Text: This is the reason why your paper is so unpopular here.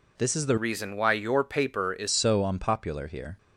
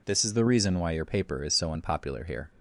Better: second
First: changes voice from "reason" to "is"; from 0.5 to 2.0 s; 1.5 s long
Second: none

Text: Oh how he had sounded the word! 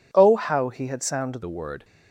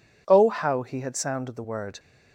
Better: second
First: changes voice at "the"; from 1.4 s on; 0.4 s long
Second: none

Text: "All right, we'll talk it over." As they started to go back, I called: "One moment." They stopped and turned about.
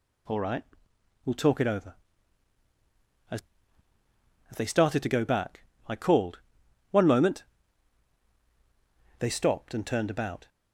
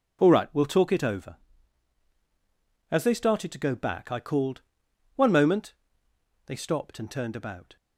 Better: second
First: says "As" twice; at 4.5 s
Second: none

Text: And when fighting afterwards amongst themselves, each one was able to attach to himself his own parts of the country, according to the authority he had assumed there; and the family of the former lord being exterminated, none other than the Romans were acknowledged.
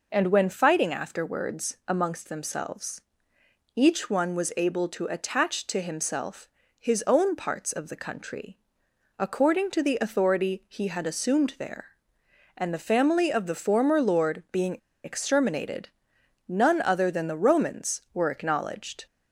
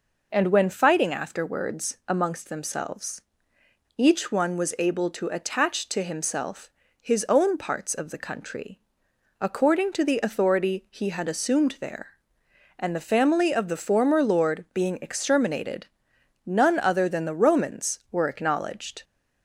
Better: second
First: pauses between "himself" and "his"; slight; at 6.4 s; 0.30 s long // pauses between "being" and "exterminated"; slight; at 14.7 s; 0.28 s long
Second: pauses between "himself" and "his"; slight; at 6.6 s; 0.30 s long

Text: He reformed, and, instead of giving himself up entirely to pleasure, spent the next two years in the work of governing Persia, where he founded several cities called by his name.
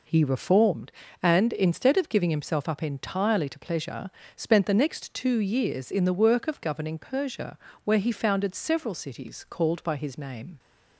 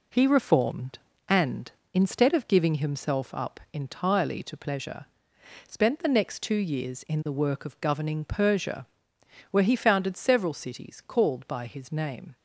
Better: neither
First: none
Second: none

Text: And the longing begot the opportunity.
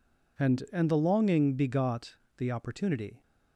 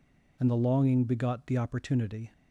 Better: second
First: says "And" twice; at 0.6 s // pauses between "begot" and "the"; slight; at 2.1 s; 0.20 s long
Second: none

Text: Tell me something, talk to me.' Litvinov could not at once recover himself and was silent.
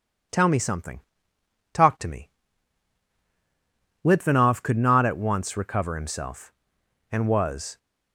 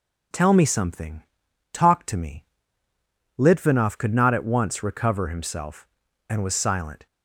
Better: second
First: stops before "silent"; at 7.7 s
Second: none

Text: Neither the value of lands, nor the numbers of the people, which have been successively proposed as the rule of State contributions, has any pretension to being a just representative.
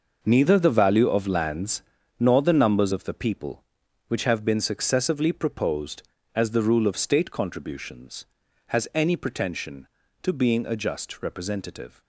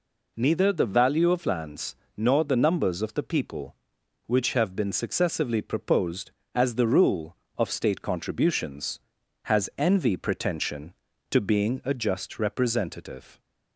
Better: first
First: none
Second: says "envy" for "any"; at 9.7 s

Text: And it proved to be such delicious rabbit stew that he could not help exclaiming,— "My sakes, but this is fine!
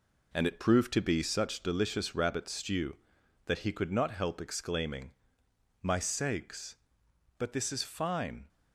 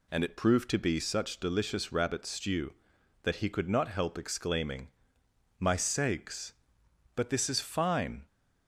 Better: second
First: gets quieter; throughout; 6.5 dB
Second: none

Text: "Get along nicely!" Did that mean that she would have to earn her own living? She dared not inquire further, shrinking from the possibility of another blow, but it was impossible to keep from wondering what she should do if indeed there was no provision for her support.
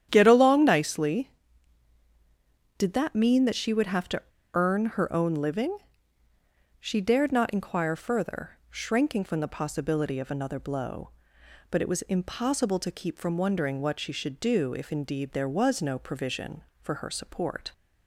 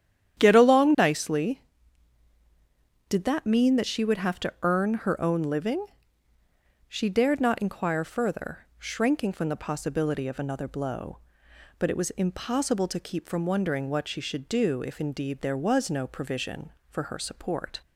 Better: second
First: starts louder than the rest; strong; until 1.1 s; 10 dB // pauses between "to" and "earn"; slight; at 4.2 s; 0.32 s long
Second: starts louder than the rest; strong; until 1.4 s; 10 dB

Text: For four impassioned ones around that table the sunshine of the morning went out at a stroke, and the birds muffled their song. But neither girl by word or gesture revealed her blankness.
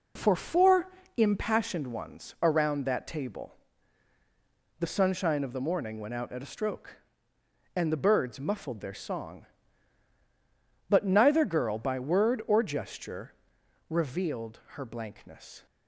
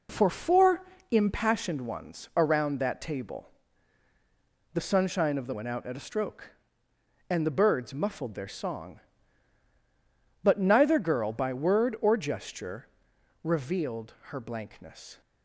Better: first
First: pauses between "four" and "impassioned"; slight; at 0.9 s; 0.28 s long // pauses between "table" and "the"; strong; at 3.5 s; 1.2 s long // pauses between "gesture" and "revealed"; noticeable; at 13.3 s; 0.56 s long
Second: pauses between "four" and "impassioned"; slight; at 0.8 s; 0.28 s long // pauses between "table" and "the"; strong; at 3.4 s; 1.2 s long // skips "morning"; at 5.5 s // pauses between "gesture" and "revealed"; noticeable; at 12.8 s; 0.56 s long

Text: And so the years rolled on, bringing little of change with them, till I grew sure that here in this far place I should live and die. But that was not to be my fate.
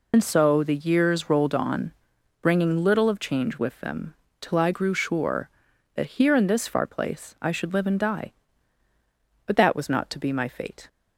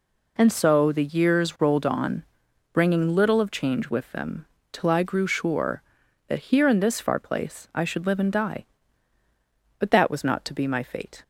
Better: second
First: loses the start of "And"; at 0.1 s; 45 ms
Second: none

